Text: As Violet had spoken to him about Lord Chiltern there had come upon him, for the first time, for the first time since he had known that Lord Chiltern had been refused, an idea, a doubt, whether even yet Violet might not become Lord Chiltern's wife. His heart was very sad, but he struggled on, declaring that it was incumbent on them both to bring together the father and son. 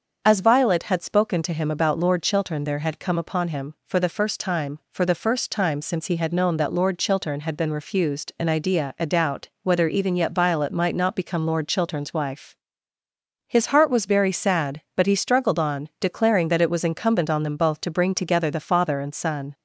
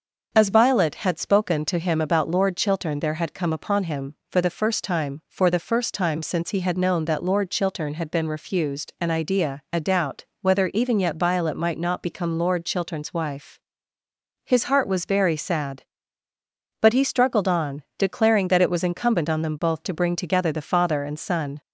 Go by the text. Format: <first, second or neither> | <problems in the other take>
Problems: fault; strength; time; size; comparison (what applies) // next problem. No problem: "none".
neither | starts louder than the rest; the same in both